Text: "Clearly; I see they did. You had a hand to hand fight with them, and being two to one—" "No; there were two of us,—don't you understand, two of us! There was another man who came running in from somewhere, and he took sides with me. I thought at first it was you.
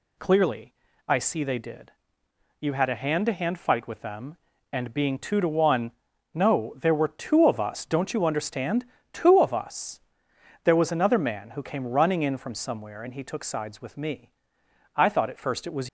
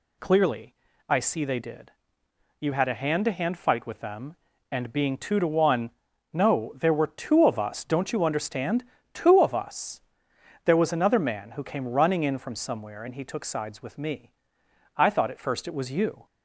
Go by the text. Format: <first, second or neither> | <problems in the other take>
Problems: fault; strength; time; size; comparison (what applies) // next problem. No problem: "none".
second | stops before "you"; at 15.8 s